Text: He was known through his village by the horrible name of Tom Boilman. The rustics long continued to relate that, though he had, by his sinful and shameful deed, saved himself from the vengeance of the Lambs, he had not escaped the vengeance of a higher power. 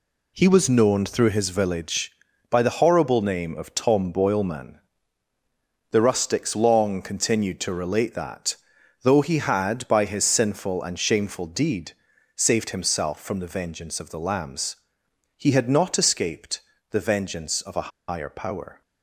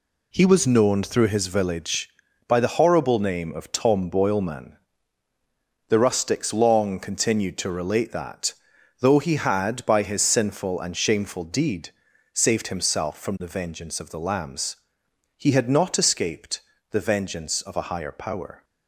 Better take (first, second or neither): second